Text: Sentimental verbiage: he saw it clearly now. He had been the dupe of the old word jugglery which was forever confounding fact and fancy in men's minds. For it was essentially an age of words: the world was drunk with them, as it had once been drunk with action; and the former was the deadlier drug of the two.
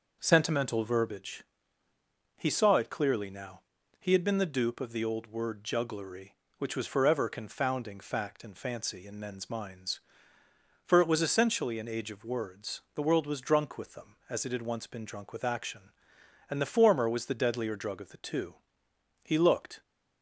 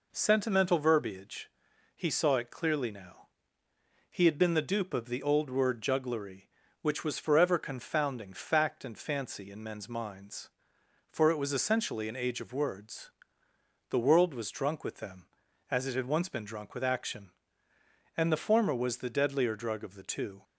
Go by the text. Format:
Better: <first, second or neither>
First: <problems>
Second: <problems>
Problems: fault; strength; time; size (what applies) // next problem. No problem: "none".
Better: second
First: goes on to say "He looked"; from 19.2 s on; 0.60 s long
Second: none